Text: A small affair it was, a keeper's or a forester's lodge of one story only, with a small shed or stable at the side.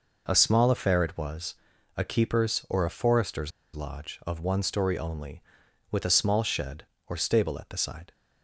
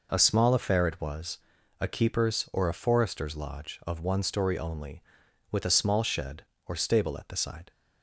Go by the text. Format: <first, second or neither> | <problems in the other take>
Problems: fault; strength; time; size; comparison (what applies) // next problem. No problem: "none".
second | pauses between "forester's" and "lodge"; slight; at 3.5 s; 0.24 s long